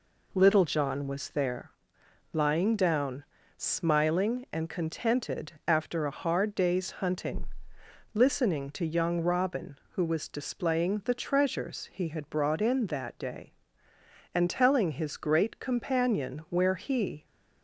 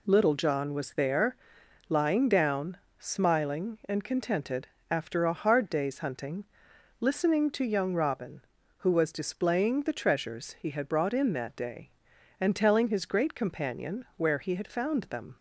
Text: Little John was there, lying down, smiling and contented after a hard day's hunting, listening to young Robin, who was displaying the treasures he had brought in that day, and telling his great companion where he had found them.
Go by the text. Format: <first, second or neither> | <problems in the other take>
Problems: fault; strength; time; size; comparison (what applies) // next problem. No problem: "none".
second | pauses between "contented" and "after"; slight; at 5.5 s; 0.16 s long; slight in the second // stops before "had found them"; at 17.2 s